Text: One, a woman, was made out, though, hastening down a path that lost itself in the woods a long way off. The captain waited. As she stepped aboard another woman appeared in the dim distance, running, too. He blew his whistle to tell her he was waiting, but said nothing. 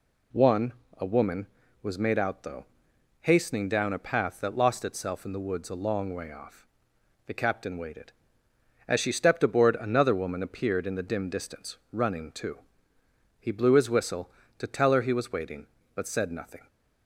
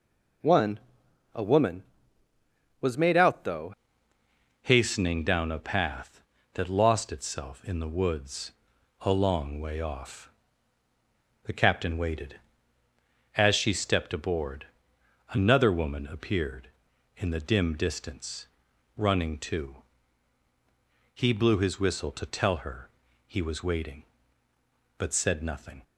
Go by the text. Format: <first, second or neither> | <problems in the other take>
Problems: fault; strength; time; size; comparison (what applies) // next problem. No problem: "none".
first | changes voice at "hastening"; from 4.6 s on; 21.2 s long // pauses between "woods" and "a"; noticeable; at 8.5 s; 0.48 s long // pauses between "aboard" and "another"; noticeable; at 14.6 s; 0.64 s long // pauses between "her" and "he"; at 22.8 s; 0.38 s long